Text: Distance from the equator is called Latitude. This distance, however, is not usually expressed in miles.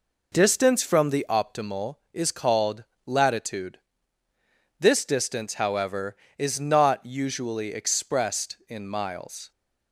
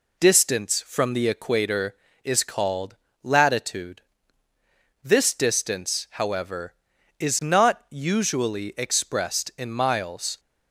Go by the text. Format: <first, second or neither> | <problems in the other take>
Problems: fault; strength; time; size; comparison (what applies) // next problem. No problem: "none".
second | says "optimal" for "equator"; at 1.2 s // pauses between "called" and "Latitude"; slight; at 2.8 s; 0.20 s long; slight in the second